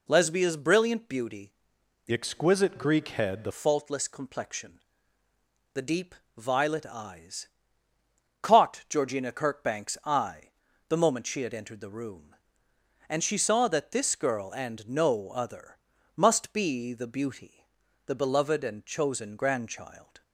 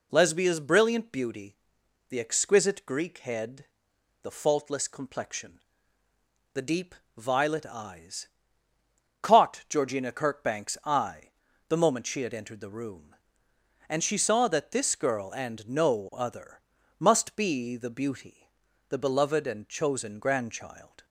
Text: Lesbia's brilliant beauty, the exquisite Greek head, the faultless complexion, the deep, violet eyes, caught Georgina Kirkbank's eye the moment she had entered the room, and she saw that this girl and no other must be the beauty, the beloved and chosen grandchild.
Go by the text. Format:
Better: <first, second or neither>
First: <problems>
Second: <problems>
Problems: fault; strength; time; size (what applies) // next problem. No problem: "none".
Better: second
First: changes voice from "exquisite" to "the"; from 2.1 to 3.5 s; 1.4 s long // pauses between "eye" and "the"; at 10.4 s; 0.38 s long // pauses between "other" and "must"; at 15.7 s; 0.38 s long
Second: pauses between "eye" and "the"; at 11.2 s; 0.38 s long // pauses between "other" and "must"; at 16.6 s; 0.38 s long